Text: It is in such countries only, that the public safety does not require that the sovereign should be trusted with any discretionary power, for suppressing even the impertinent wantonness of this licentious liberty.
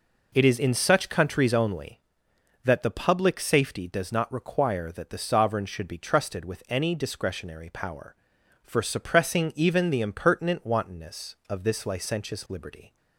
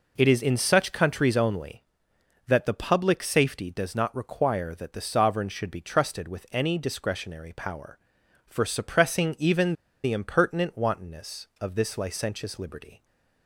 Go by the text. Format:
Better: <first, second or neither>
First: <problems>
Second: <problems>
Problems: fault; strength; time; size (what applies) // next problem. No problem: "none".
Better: first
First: none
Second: pauses between "even" and "the"; slight; at 9.7 s; 0.31 s long